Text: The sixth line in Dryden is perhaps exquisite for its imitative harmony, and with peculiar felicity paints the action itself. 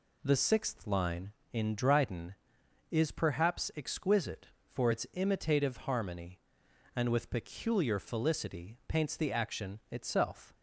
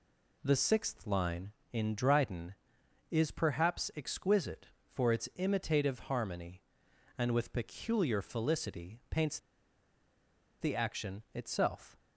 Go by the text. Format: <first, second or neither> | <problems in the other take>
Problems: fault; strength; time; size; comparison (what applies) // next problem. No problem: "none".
first | pauses between "paints" and "the"; at 9.3 s; 1.2 s long